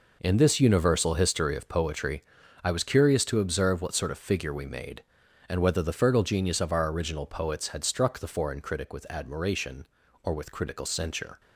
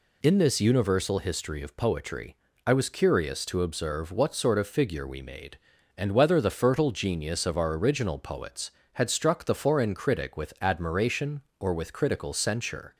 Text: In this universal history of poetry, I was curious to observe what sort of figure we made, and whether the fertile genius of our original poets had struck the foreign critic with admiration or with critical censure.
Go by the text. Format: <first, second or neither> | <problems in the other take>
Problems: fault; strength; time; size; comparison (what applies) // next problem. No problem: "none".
second | gets quieter; strong; throughout; 10.5 dB